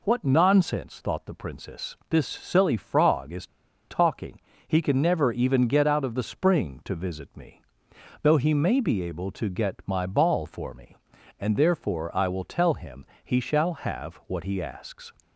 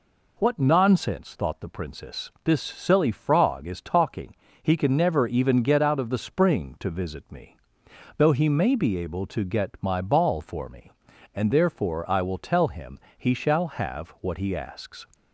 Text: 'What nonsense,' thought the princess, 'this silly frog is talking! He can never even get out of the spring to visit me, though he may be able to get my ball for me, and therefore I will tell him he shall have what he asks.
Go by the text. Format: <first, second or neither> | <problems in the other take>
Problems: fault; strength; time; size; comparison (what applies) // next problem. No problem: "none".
second | pauses between "is" and "talking"; at 3.4 s; 0.42 s long // pauses between "him" and "he"; slight; at 13.0 s; 0.18 s long; slight in the second